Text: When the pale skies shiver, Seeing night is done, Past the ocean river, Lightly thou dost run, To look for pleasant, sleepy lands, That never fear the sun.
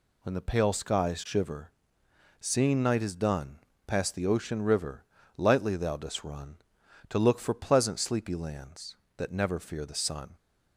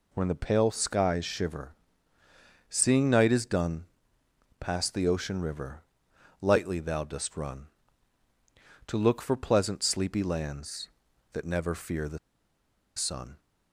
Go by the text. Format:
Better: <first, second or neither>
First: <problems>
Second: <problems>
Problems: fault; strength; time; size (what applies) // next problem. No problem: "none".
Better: first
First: none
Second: pauses between "the" and "sun"; noticeable; at 12.1 s; 0.78 s long